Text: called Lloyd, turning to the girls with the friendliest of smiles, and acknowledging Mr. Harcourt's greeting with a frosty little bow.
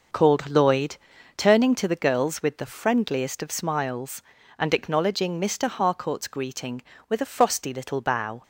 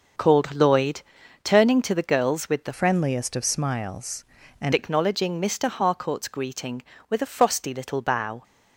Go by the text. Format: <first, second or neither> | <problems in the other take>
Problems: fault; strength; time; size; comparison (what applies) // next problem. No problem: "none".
first | changes voice from "friendliest" to "and"; from 2.7 to 4.7 s; 2.0 s long